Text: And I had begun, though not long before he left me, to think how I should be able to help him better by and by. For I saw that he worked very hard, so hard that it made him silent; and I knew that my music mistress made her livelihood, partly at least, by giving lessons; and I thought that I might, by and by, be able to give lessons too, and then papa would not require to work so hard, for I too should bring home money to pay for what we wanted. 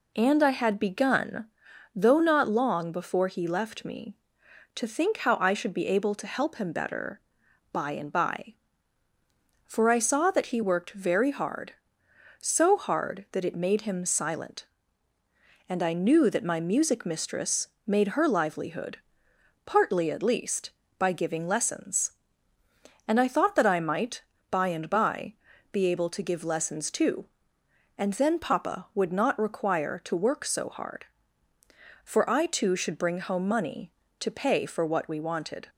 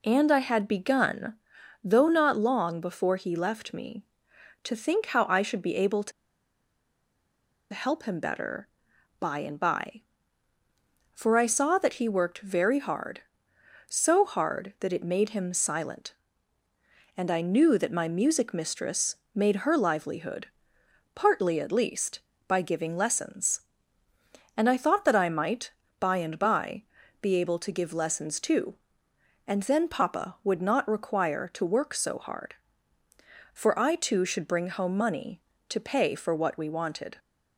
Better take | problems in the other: first | pauses between "to" and "help"; strong; at 6.1 s; 1.6 s long // pauses between "mistress" and "made"; slight; at 19.1 s; 0.18 s long; slight in the first

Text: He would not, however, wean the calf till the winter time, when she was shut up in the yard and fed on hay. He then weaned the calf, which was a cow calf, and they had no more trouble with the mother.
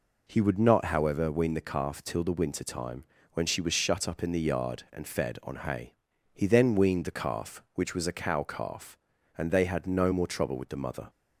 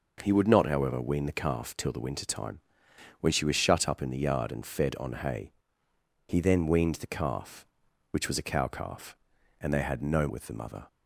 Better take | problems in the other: first | skips "more trouble"; at 10.2 s

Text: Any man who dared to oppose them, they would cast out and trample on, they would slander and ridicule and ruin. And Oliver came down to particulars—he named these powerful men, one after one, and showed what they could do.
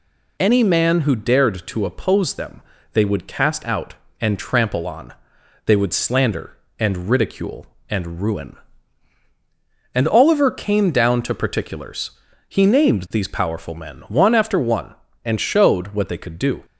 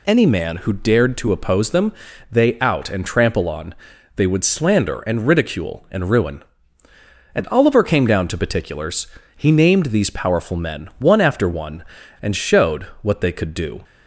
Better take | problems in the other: first | skips "would cast"; at 2.5 s // pauses between "showed" and "what"; slight; at 12.8 s; 0.18 s long

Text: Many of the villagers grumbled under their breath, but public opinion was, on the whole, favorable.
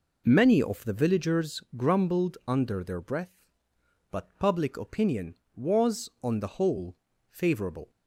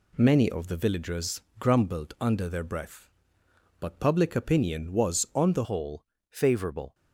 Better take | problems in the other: first | pauses between "villagers" and "grumbled"; slight; at 1.4 s; 0.16 s long; slight in the first // changes voice at "whole"; from 5.6 s on; 1.3 s long

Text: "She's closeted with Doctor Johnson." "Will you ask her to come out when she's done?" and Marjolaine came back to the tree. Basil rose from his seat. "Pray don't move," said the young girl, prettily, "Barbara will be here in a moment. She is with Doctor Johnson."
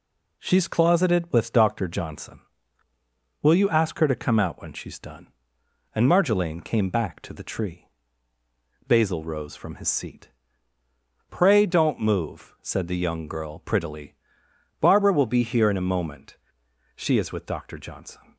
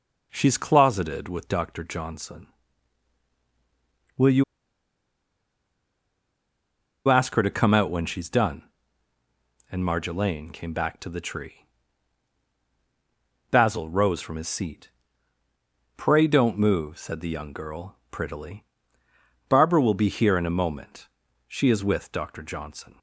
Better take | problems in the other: first | pauses between "you" and "ask"; strong; at 4.4 s; 2.6 s long

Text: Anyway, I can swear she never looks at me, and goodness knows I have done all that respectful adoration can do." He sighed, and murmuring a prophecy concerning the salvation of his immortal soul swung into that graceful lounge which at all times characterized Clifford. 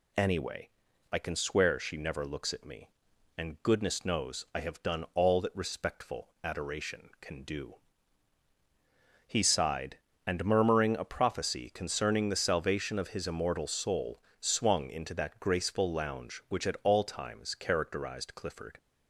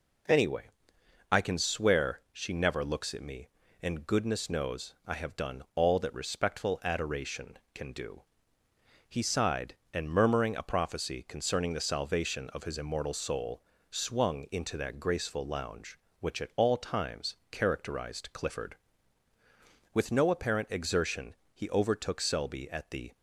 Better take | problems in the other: first | pauses between "soul" and "swung"; slight; at 13.6 s; 0.26 s long; slight in the first // pauses between "times" and "characterized"; slight; at 17.3 s; 0.16 s long // goes on to say "With no apparent exertion he overtook Selby at the"; strong; from 19.9 s on; 3.2 s long

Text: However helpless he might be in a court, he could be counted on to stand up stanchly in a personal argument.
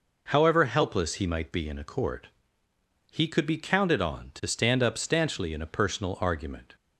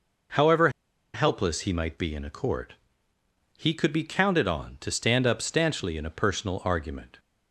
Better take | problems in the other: first | pauses between "However" and "helpless"; at 0.6 s; 0.45 s long

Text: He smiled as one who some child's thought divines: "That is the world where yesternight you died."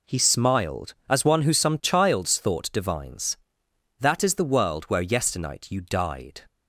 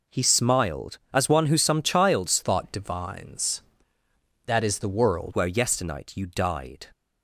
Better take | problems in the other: first | changes voice from "thought" to "world"; from 2.4 to 5.3 s; 2.9 s long

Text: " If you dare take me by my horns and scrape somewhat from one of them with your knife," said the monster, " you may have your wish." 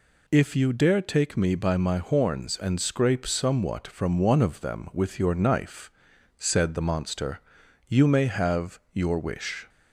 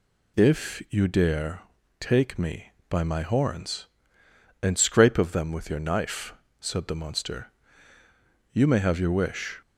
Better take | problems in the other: first | pauses between "dare" and "take"; at 1.6 s; 0.40 s long // skips "somewhat from one"; at 5.1 s

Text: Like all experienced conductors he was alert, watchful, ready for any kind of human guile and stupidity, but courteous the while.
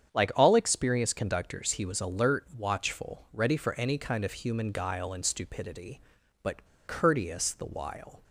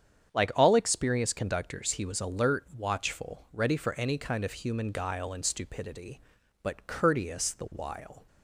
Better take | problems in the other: second | starts louder than the rest; strong; until 1.1 s; 8 dB; strong in the second // pauses between "but" and "courteous"; slight; at 6.6 s; 0.21 s long

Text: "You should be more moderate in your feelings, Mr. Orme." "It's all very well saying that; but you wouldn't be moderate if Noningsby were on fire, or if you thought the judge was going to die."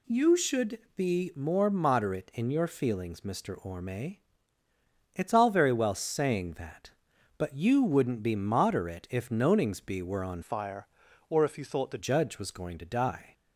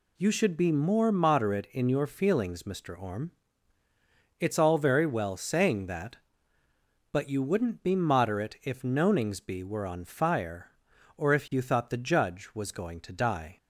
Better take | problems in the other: second | pauses between "should" and "be"; slight; at 0.7 s; 0.18 s long // changes voice from "fire" to "the"; from 10.4 to 11.9 s; 1.5 s long

